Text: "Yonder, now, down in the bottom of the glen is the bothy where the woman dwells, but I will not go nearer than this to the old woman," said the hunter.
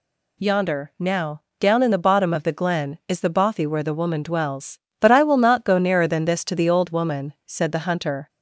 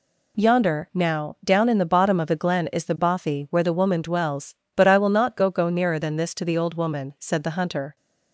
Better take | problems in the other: first | says "go" twice; at 5.4 s

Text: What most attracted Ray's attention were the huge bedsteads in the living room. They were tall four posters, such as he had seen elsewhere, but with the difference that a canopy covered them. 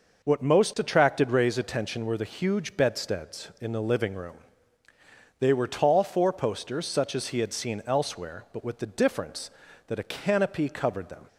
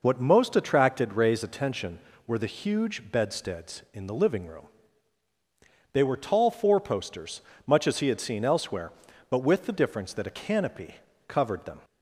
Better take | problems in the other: first | says "much" for "such"; at 7.6 s // pauses between "canopy" and "covered"; slight; at 10.9 s; 0.32 s long

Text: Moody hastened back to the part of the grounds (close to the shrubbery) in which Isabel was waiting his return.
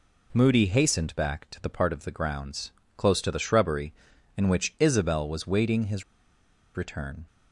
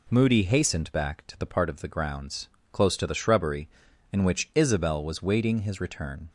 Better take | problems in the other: second | pauses between "his" and "return"; noticeable; at 6.0 s; 0.72 s long

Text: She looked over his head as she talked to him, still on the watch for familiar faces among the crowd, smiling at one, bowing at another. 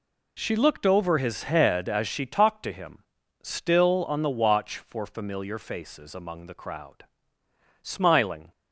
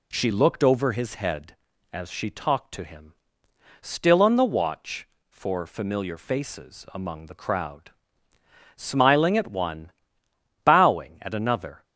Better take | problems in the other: second | stops before "at one bowing at another"; at 8.5 s

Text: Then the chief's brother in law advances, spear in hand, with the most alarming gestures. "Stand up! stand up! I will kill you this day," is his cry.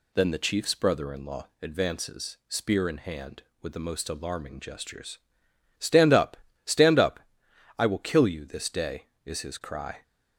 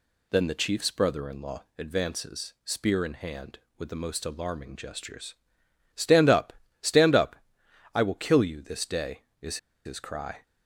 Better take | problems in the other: first | pauses between "law" and "advances"; slight; at 1.6 s; 0.16 s long; slight in the first // pauses between "is" and "his"; slight; at 9.5 s; 0.28 s long

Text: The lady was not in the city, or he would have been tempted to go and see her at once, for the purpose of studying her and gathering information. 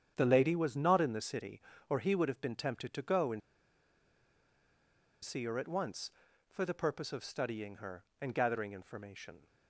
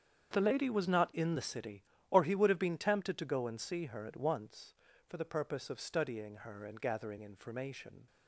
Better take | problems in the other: second | starts louder than the rest; strong; until 1.1 s; 8.5 dB; strong in the second // pauses between "and" and "see"; strong; at 3.4 s; 1.8 s long

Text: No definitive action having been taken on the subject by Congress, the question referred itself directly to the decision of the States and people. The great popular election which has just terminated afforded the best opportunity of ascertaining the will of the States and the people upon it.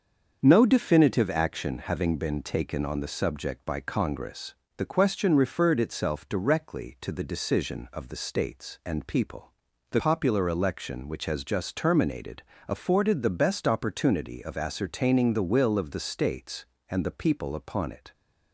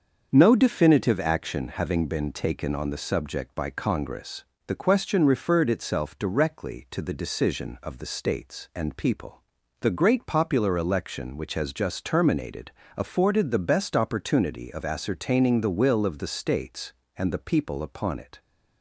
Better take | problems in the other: second | starts louder than the rest; until 1.4 s; 6.5 dB; also in the second // skips "great"; at 9.9 s // pauses between "terminated" and "afforded"; slight; at 12.4 s; 0.26 s long; slight in the second

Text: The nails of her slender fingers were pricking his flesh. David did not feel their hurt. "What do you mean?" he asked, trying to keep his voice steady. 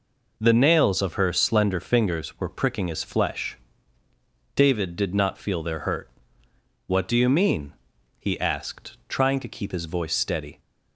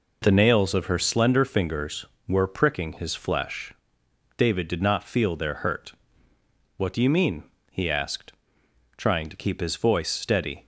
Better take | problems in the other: neither | none

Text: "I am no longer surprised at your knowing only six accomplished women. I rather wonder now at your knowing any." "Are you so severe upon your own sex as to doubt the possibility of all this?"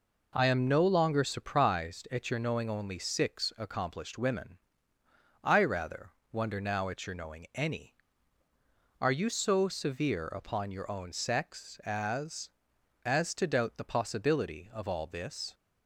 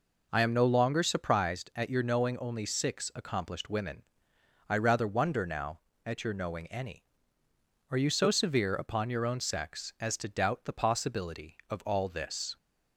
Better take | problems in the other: second | pauses between "rather" and "wonder"; slight; at 6.0 s; 0.22 s long // says "as" twice; at 13.0 s

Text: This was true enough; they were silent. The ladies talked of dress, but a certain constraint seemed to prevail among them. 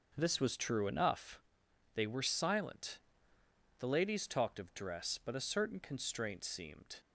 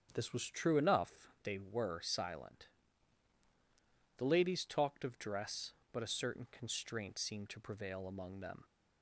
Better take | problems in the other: second | starts louder than the rest; until 1.1 s; 7 dB; strong in the second // stops before "to prevail among them"; at 7.0 s

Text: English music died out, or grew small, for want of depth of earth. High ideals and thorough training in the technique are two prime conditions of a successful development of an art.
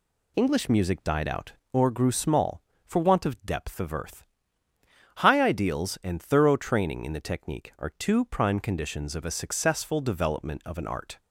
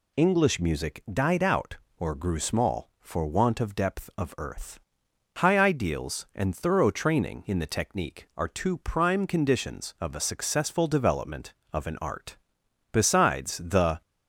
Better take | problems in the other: first | goes on to say "Besides the"; noticeable; from 12.9 s on; 1.1 s long

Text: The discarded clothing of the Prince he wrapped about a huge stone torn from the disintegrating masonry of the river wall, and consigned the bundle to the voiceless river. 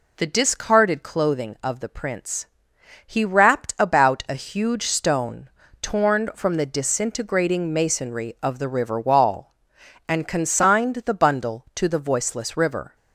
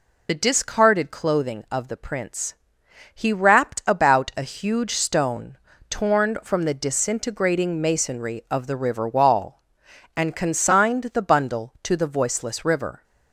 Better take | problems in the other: first | loses the start of "The"; at 0.2 s; 40 ms // pauses between "Prince" and "he"; noticeable; at 2.5 s; 0.60 s long; noticeable in the first // pauses between "stone" and "torn"; slight; at 5.5 s; 0.32 s long; slight in the first

